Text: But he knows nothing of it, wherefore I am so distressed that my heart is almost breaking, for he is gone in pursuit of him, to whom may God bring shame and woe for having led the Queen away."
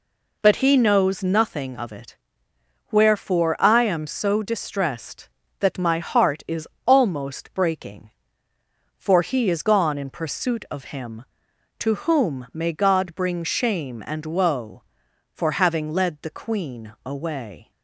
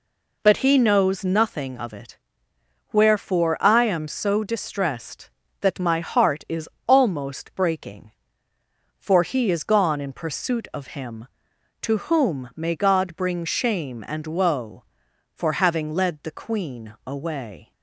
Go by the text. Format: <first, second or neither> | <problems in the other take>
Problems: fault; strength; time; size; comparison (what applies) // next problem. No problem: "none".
neither | pauses between "is" and "almost"; slight; the same in both